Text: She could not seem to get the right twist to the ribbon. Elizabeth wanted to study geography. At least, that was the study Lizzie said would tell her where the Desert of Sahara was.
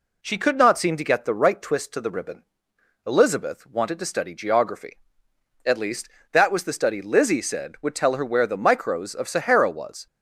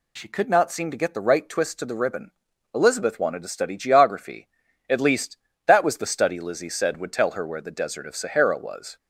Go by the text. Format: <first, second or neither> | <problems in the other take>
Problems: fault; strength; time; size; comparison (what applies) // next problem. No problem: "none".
second | says "Micros" for "Desert"; at 8.5 s